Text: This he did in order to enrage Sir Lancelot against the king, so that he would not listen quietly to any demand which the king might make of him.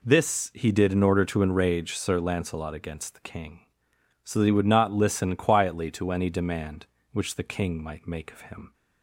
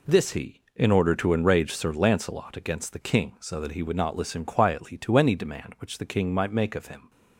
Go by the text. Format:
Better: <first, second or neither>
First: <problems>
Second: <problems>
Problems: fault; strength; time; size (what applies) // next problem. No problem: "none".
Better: first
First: none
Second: skips "did"; at 0.6 s